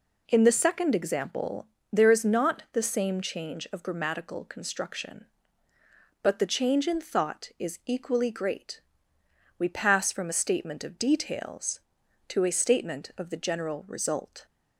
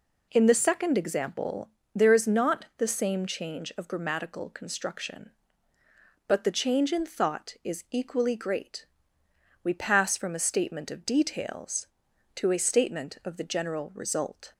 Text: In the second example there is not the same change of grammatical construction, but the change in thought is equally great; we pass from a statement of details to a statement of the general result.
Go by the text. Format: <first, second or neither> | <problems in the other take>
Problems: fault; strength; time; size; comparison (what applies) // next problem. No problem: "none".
neither | pauses between "example" and "there"; slight; the same in both